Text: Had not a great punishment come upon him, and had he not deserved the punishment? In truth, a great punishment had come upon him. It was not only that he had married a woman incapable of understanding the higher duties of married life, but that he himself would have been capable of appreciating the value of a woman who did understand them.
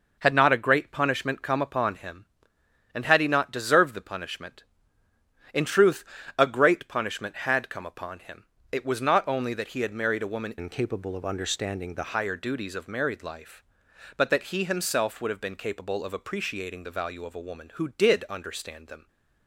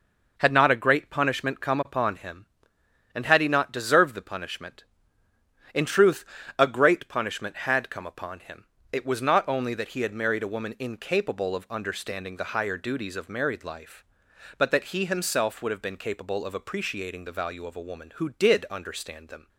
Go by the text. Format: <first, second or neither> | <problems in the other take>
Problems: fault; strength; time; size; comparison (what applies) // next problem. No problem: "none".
second | changes voice from "incapable" to "the"; from 10.5 to 12.1 s; 1.6 s long